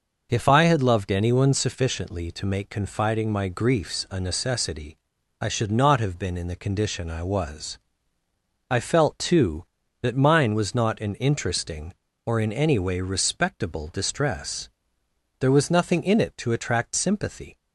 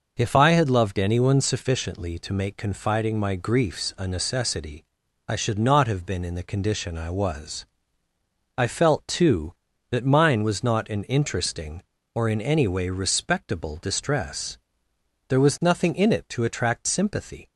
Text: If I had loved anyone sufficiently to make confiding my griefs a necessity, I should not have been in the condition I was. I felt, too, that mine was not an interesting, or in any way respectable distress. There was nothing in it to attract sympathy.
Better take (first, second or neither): neither